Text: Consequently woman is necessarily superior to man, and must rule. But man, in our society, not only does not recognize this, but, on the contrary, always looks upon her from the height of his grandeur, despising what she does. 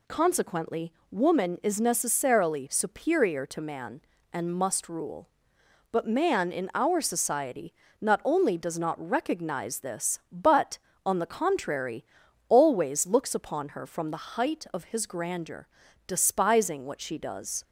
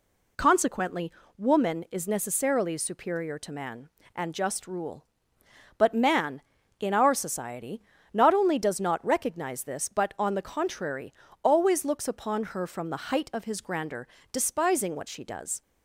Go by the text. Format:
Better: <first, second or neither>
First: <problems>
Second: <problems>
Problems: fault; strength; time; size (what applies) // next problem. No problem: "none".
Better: first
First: pauses between "Consequently" and "woman"; slight; at 0.9 s; 0.18 s long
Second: pauses between "Consequently" and "woman"; slight; at 1.1 s; 0.26 s long // says "just" for "must"; at 4.3 s